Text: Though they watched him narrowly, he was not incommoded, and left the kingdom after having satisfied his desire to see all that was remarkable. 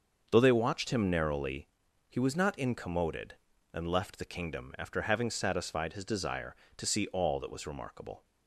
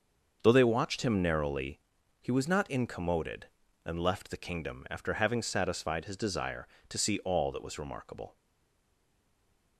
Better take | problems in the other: first | starts louder than the rest; until 1.4 s; 6.5 dB; also in the first // stays silent after the last word; noticeable; from 8.3 s on; 1.4 s long

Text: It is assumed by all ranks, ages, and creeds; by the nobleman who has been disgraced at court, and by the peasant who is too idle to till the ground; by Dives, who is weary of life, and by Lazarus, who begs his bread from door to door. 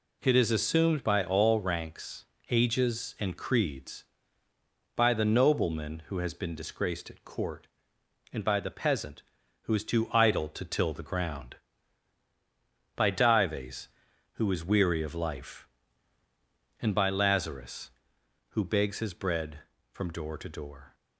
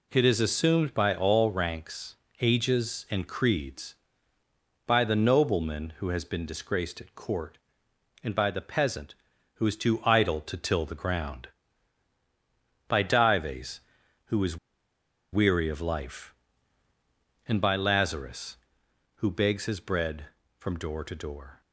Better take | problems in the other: first | pauses between "is" and "weary"; noticeable; at 14.5 s; 0.76 s long

